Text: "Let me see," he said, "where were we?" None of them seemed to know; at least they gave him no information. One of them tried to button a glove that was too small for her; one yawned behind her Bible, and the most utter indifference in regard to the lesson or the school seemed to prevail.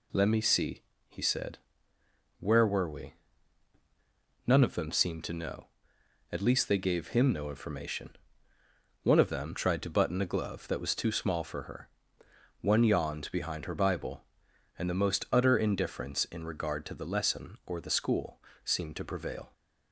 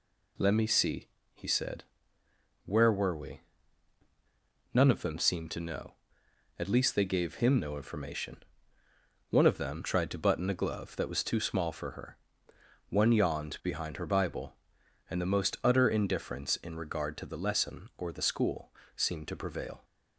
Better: neither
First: pauses between "school" and "seemed"; slight; at 18.4 s; 0.24 s long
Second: pauses between "school" and "seemed"; slight; at 18.7 s; 0.24 s long

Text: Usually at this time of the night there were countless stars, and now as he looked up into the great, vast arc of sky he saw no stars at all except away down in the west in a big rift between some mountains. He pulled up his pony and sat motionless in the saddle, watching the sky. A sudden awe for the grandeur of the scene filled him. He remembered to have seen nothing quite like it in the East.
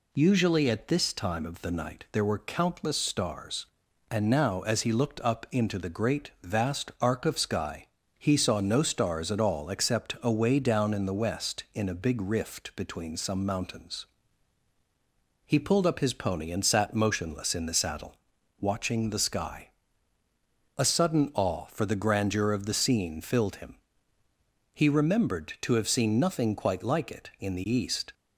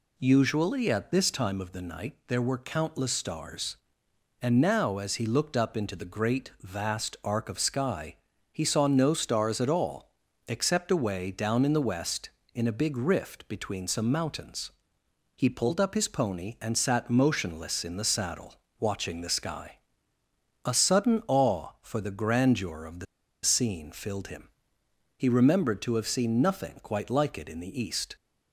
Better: first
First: pauses between "sky" and "he"; slight; at 7.8 s; 0.32 s long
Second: pauses between "sky" and "he"; slight; at 8.1 s; 0.36 s long // pauses between "all" and "except"; at 10.0 s; 0.38 s long // pauses between "the" and "scene"; at 23.0 s; 0.38 s long

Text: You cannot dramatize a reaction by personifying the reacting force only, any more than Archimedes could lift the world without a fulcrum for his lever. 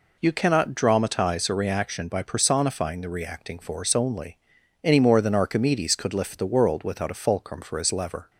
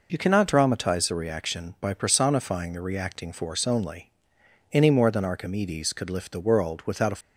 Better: first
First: none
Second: stops before "fulcrum for his lever"; at 7.2 s

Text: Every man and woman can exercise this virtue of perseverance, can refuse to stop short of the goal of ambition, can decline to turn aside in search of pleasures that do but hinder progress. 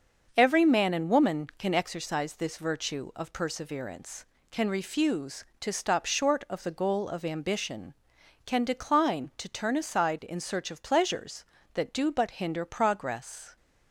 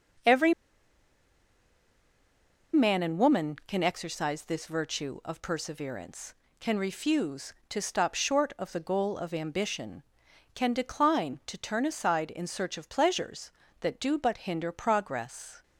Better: first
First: starts louder than the rest; until 1.3 s; 6.5 dB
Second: starts louder than the rest; until 3.4 s; 6.5 dB // pauses between "Every" and "man"; strong; at 0.5 s; 2.2 s long

